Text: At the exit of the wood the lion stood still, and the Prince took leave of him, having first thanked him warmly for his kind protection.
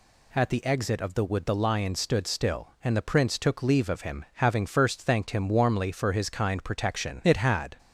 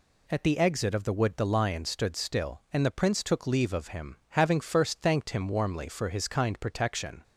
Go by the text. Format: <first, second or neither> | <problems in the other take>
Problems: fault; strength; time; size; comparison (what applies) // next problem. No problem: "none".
second | goes on to say "It had"; from 7.2 s on; 0.54 s long